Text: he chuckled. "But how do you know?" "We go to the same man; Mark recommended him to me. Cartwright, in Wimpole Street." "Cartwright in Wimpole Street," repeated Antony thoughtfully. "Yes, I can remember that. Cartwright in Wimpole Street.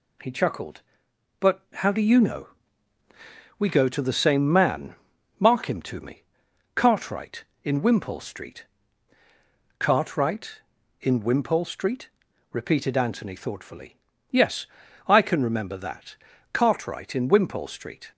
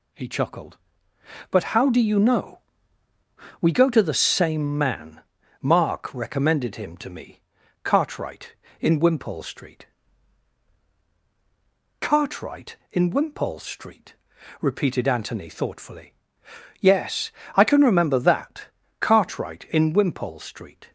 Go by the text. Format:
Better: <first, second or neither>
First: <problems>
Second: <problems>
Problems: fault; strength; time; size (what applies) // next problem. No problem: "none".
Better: second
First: pauses between "But" and "how"; slight; at 1.6 s; 0.16 s long // skips "recommended"; at 5.6 s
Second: none